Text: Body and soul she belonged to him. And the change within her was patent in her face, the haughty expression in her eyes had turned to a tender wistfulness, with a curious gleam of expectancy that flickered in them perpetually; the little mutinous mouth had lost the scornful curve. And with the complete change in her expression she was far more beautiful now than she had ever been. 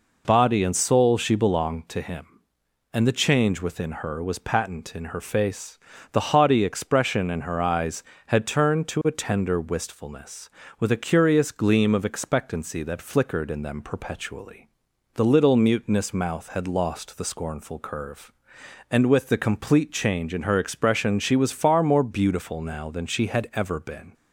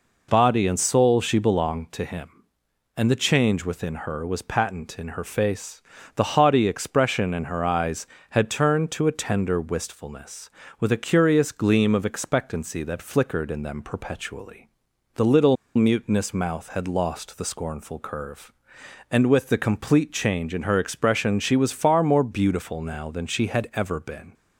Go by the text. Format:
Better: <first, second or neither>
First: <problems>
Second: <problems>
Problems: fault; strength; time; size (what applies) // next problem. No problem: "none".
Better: first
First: none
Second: pauses between "little" and "mutinous"; slight; at 15.5 s; 0.20 s long